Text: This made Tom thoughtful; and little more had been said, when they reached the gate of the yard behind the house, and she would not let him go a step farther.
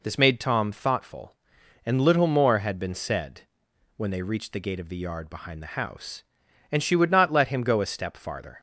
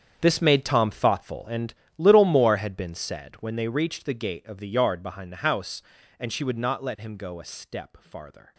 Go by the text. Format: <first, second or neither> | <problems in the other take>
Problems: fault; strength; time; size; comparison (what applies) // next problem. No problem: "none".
first | gets quieter; strong; throughout; 15 dB // pauses between "and" and "little"; slight; at 1.7 s; 0.24 s long